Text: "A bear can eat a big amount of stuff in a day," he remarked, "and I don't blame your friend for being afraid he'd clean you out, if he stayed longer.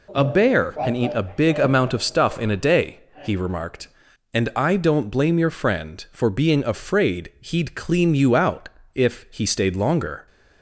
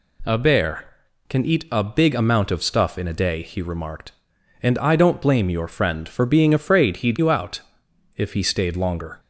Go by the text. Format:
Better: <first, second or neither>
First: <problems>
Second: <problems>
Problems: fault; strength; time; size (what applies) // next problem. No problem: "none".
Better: first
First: none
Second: skips "clean"; at 7.1 s